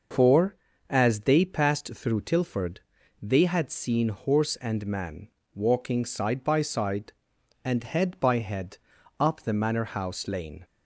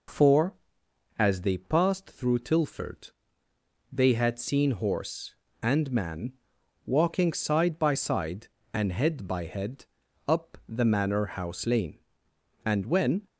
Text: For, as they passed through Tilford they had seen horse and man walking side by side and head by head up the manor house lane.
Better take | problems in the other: first | pauses between "Tilford" and "they"; noticeable; at 3.1 s; 0.82 s long; also in the first // pauses between "man" and "walking"; noticeable; at 6.3 s; 0.54 s long; slight in the first // pauses between "head" and "up"; at 9.8 s; 0.42 s long; also in the first // goes on to say "And when"; noticeable; from 12.6 s on; 0.62 s long

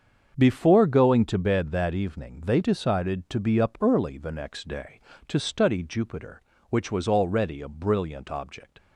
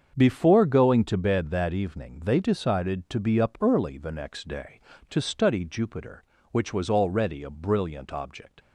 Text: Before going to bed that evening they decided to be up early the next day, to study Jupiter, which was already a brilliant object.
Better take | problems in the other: neither | starts louder than the rest; the same in both

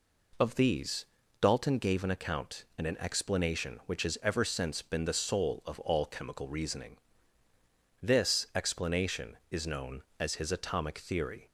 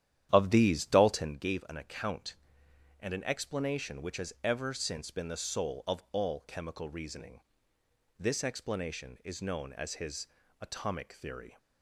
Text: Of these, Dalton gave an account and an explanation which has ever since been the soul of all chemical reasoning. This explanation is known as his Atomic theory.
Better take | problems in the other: first | starts louder than the rest; strong; until 1.4 s; 11 dB // pauses between "his" and "Atomic"; slight; at 10.2 s; 0.32 s long

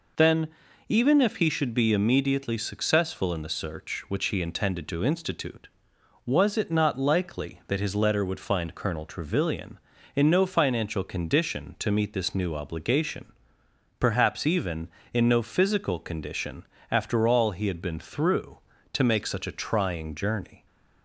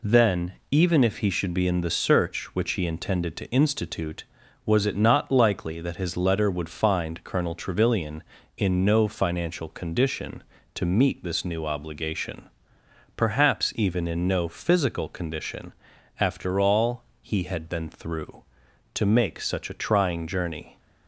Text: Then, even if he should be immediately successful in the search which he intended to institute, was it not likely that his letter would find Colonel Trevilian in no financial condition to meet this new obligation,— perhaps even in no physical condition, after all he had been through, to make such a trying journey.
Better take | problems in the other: first | skips "immediately successful"; at 1.6 s // pauses between "all" and "he"; slight; at 17.0 s; 0.18 s long

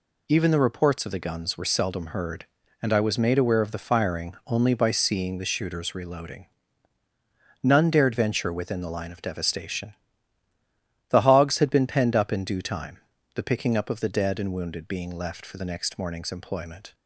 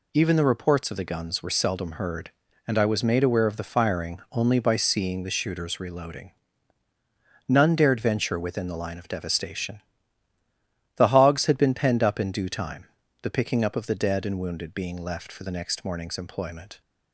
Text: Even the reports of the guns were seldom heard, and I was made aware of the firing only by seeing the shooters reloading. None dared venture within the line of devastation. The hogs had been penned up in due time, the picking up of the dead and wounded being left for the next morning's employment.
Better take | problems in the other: neither | none

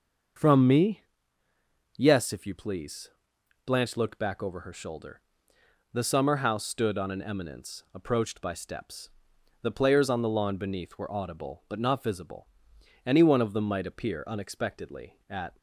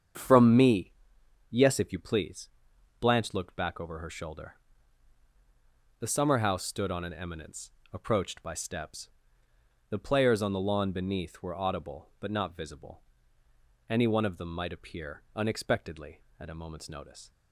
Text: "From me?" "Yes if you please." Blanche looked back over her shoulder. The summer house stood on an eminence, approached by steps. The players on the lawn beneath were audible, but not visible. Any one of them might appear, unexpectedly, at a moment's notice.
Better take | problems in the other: second | starts louder than the rest; until 2.3 s; 6.5 dB; strong in the second // stops before "a moment's notice"; at 15.5 s

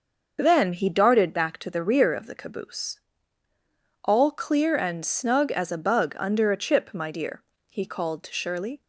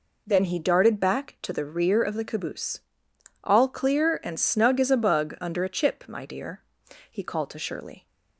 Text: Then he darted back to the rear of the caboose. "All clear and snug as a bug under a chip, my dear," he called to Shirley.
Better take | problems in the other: second | loses the start of "Then"; at 0.3 s; 25 ms

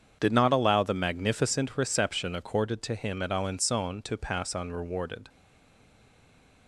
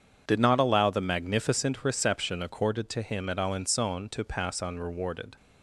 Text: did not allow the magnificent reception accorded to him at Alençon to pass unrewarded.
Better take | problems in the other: second | starts louder than the rest; strong; until 1.2 s; 7.5 dB; strong in the second // stays silent after the last word; noticeable; from 5.2 s on; 1.4 s long

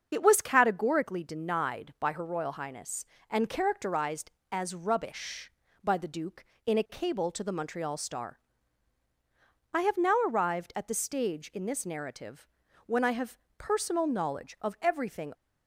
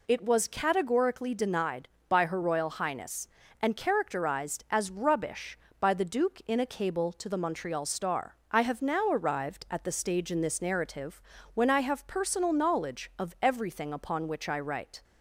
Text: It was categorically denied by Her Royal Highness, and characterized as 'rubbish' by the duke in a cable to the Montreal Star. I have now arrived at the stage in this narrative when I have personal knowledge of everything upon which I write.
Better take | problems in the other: second | starts louder than the rest; until 1.1 s; 7 dB // pauses between "narrative" and "when"; at 12.4 s; 0.40 s long; slight in the second // pauses between "have" and "personal"; slight; at 13.3 s; 0.22 s long // stops before "upon which I write"; at 15.3 s

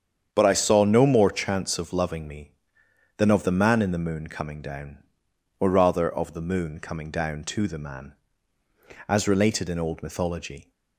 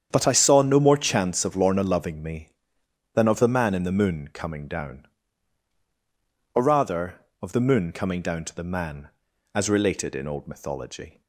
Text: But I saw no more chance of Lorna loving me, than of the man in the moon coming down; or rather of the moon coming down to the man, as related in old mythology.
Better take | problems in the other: second | starts louder than the rest; strong; until 1.3 s; 8 dB; strong in the second // skips "Lorna"; at 1.9 s

